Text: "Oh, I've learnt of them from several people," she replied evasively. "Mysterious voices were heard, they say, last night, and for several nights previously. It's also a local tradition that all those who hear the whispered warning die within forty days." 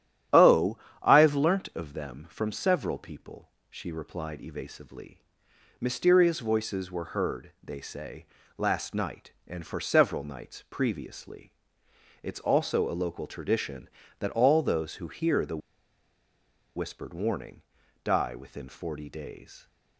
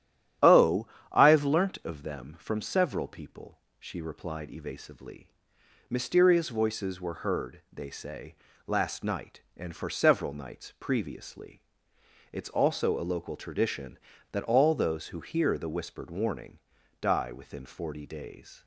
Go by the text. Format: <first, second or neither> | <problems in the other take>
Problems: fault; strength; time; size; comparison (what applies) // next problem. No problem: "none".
second | starts louder than the rest; strong; until 1.5 s; 12 dB; strong in the second // pauses between "the" and "whispered"; at 15.5 s; 1.1 s long // pauses between "warning" and "die"; at 17.6 s; 0.42 s long; also in the second